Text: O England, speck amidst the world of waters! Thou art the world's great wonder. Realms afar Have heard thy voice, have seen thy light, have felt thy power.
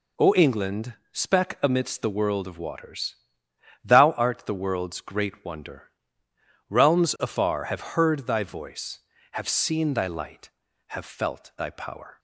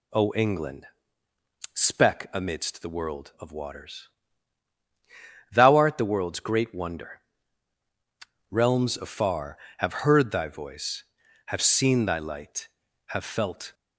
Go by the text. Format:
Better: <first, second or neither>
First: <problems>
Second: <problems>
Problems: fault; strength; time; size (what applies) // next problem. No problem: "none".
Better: first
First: none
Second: stops before "thy power"; at 13.7 s